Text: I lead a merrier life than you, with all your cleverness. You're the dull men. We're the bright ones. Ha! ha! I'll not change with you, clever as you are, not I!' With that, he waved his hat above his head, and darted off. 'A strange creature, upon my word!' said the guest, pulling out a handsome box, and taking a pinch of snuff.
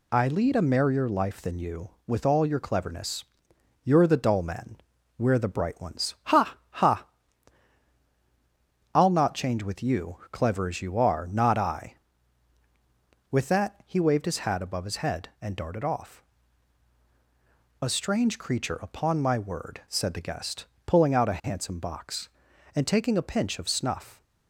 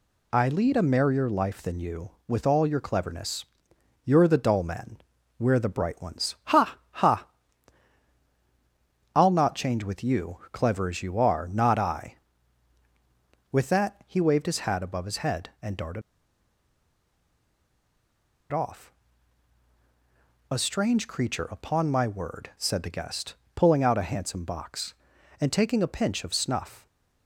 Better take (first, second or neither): first